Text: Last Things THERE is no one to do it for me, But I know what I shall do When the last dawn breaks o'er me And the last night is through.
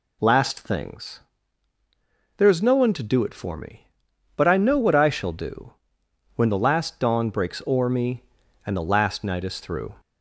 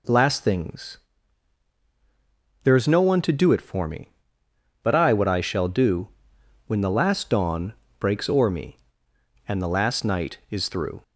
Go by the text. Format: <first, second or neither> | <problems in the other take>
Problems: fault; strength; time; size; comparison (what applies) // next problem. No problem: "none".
first | pauses between "Things" and "THERE"; strong; at 0.9 s; 1.6 s long; also in the first // skips "know"; at 5.1 s // pauses between "do" and "When"; noticeable; at 6.0 s; 0.58 s long; noticeable in the first // pauses between "dawn" and "breaks"; slight; at 7.7 s; 0.24 s long